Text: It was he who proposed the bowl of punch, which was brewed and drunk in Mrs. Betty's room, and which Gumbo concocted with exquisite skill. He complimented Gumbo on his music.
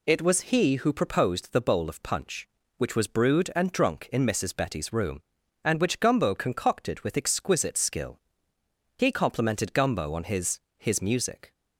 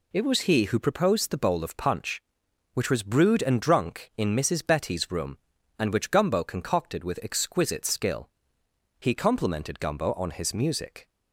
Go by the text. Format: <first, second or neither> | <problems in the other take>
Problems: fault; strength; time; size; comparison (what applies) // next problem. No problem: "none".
second | says "his" twice; at 10.7 s